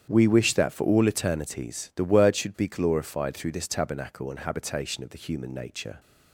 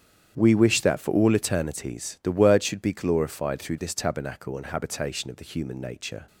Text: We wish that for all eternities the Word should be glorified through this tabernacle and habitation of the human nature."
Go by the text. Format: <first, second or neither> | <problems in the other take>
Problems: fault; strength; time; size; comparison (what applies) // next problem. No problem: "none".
neither | starts louder than the rest; strong; the same in both